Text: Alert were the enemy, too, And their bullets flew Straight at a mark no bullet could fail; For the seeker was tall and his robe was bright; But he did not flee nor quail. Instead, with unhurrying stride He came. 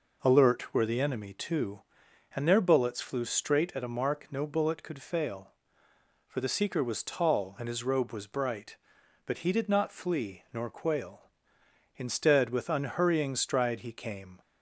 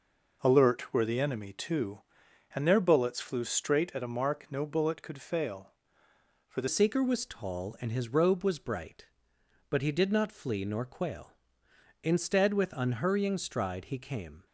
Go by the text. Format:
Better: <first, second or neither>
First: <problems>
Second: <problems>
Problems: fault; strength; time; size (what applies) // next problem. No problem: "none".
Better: first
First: none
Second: changes voice at "seeker"; from 6.6 s on; 7.8 s long